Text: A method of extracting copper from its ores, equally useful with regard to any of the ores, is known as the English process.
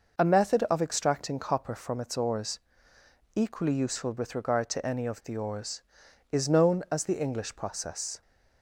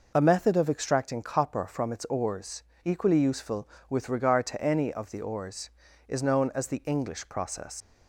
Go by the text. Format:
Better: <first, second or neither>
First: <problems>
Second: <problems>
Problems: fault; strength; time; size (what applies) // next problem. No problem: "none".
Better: first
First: none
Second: leaves "process" unfinished; at 7.8 s; 80 ms